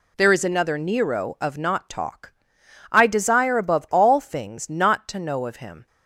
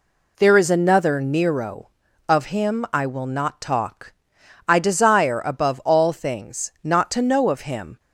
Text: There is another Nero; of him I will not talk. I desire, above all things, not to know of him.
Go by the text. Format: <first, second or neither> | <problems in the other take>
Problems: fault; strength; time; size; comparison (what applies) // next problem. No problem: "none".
second | skips "him I will"; at 1.5 s